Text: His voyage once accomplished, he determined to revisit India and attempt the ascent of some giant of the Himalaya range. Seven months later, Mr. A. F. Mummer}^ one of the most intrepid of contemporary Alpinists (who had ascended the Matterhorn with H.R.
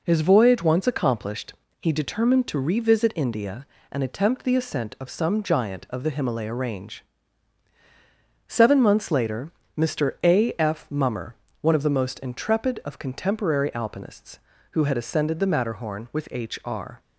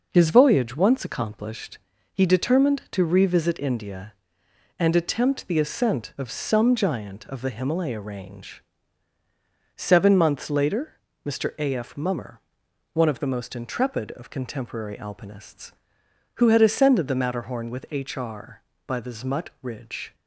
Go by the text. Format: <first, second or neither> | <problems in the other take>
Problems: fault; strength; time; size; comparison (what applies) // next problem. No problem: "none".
first | goes on to say "by the Zmutt ridge"; noticeable; from 18.8 s on; 1.2 s long